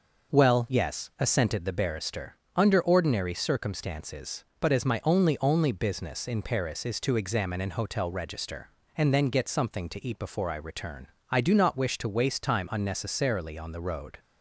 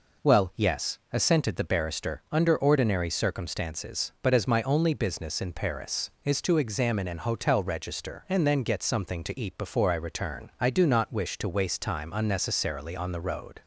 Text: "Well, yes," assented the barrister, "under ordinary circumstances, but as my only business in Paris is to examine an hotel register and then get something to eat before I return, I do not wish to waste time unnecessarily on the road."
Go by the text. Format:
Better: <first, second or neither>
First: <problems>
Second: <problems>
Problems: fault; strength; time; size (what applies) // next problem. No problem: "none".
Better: second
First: says "only" twice; at 5.4 s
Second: none